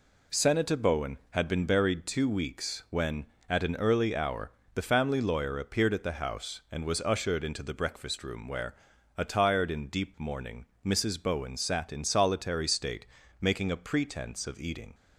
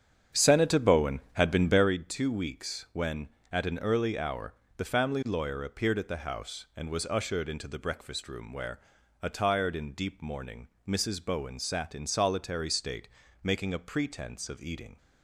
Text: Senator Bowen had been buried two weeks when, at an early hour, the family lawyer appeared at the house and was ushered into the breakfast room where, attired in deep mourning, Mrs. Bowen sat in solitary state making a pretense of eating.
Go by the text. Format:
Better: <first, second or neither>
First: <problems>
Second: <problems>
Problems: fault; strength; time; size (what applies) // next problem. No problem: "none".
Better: first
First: pauses between "state" and "making"; at 13.0 s; 0.38 s long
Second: starts louder than the rest; strong; until 1.9 s; 8 dB // pauses between "state" and "making"; at 13.0 s; 0.38 s long